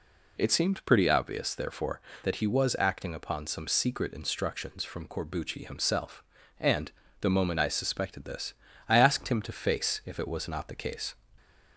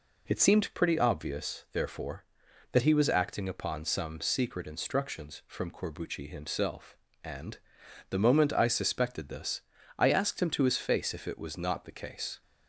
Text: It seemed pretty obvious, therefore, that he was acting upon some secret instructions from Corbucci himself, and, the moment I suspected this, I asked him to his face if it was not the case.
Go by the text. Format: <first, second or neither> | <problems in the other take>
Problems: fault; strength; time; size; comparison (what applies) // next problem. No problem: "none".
second | skips "his"; at 9.5 s